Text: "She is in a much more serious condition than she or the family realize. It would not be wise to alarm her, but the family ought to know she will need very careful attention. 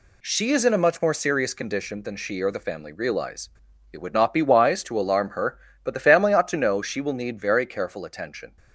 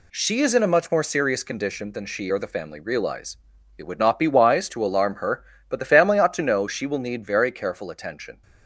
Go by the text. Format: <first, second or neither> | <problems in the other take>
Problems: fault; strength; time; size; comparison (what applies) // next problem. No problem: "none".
neither | none